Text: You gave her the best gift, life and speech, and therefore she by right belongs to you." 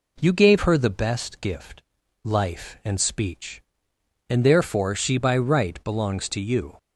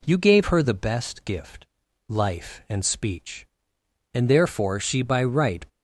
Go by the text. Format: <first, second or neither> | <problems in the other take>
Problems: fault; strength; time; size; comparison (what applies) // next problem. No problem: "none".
first | stops before "belongs to you"; at 5.6 s